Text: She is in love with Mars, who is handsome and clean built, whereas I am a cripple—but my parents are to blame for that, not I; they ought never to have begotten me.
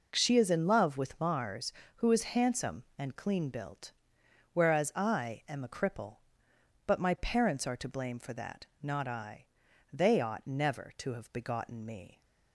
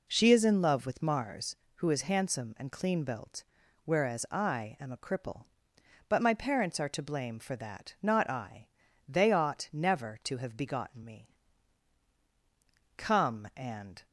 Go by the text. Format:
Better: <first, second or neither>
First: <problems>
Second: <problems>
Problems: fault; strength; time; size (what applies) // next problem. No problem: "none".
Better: first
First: none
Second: goes on to say "Come and"; noticeable; from 12.9 s on; 1.0 s long